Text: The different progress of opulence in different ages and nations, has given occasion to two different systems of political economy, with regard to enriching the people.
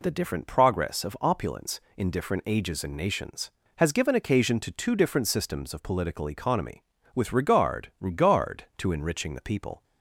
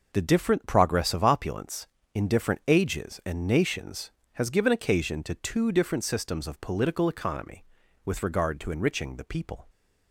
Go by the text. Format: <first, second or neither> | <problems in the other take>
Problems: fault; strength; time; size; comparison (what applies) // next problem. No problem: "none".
second | says "regard" twice; at 7.9 s